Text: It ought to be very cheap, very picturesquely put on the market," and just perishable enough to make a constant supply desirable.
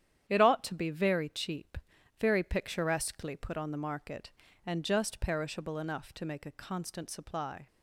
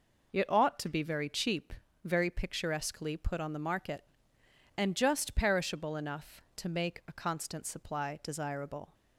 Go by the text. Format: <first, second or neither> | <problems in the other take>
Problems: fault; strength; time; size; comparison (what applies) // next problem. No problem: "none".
second | starts louder than the rest; strong; until 1.3 s; 10 dB // stops before "desirable"; at 7.6 s